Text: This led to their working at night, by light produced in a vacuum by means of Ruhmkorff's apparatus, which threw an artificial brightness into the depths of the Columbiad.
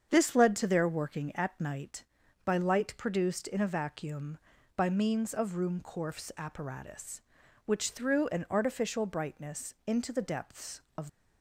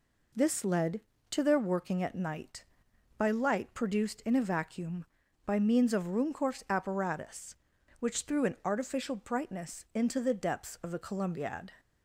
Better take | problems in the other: second | starts louder than the rest; strong; until 1.1 s; 7.5 dB // stops before "the Columbiad"; at 11.0 s

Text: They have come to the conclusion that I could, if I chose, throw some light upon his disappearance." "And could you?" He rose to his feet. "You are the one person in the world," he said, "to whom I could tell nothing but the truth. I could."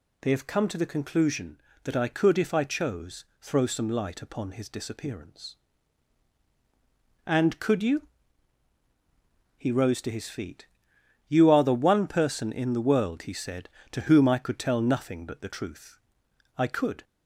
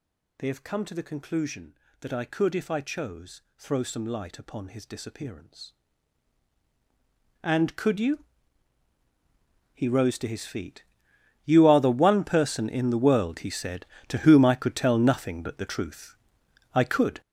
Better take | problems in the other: first | gets louder; strong; throughout; 10 dB

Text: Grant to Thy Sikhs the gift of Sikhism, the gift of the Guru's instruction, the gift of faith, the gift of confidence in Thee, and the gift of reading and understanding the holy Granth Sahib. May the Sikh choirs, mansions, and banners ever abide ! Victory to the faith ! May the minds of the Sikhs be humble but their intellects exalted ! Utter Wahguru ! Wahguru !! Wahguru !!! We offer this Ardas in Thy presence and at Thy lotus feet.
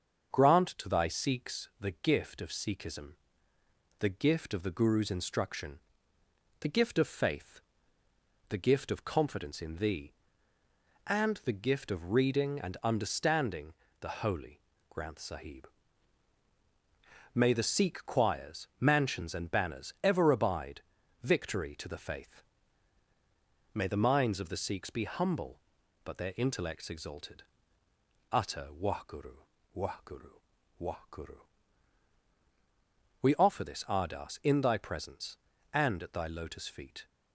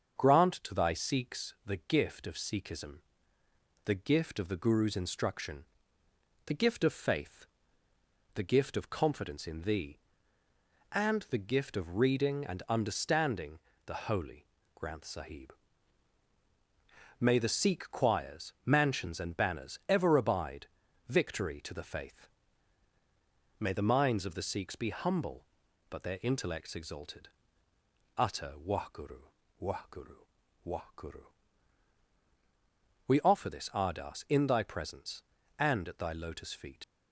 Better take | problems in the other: first | starts louder than the rest; strong; until 1.2 s; 7 dB; strong in the first // pauses between "understanding" and "the"; slight; at 13.5 s; 0.26 s long; slight in the first // pauses between "holy" and "Granth"; slight; at 14.4 s; 0.36 s long; slight in the first // leaves "feet" unfinished; at 36.8 s; 65 ms

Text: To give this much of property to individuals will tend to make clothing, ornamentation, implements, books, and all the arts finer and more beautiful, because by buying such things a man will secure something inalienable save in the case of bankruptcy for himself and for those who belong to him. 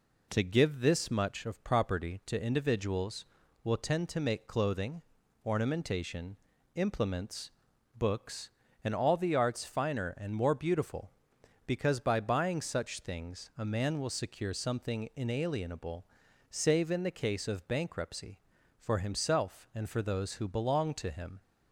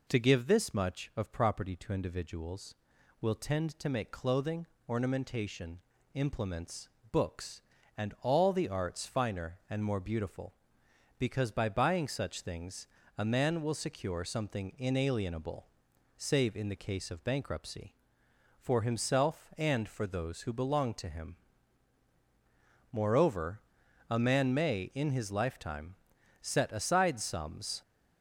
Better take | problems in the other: first | pauses between "things" and "a"; slight; at 12.8 s; 0.30 s long // pauses between "inalienable" and "save"; noticeable; at 15.6 s; 0.52 s long; noticeable in the first // goes on to say "Moreover a man may in his lifetime set aside sums"; strong; from 22.9 s on; 4.9 s long

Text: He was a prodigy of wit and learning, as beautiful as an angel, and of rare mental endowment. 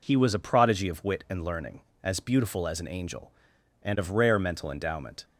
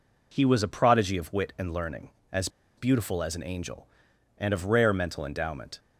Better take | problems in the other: first | pauses between "as" and "beautiful"; slight; at 2.4 s; 0.28 s long

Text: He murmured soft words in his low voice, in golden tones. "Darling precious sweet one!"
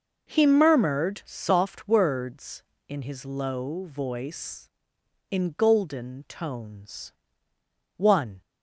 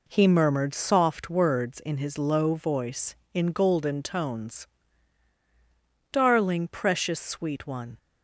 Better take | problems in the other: second | skips "Darling precious sweet"; at 7.5 s

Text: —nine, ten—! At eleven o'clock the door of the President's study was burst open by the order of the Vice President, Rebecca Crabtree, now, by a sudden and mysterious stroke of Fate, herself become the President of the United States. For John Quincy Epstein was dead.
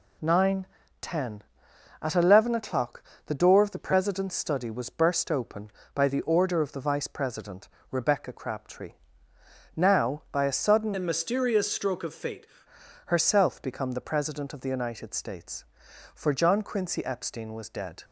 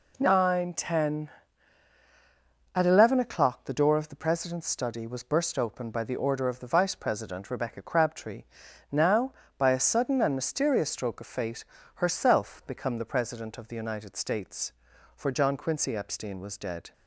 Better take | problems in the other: second | pauses between "o'clock" and "the"; slight; at 3.0 s; 0.26 s long // changes voice from "and" to "Fate"; from 10.9 to 12.4 s; 1.5 s long

